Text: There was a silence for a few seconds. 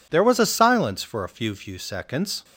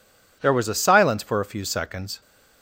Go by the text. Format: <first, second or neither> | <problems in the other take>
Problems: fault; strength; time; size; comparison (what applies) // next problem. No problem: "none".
second | says "few" twice; at 1.5 s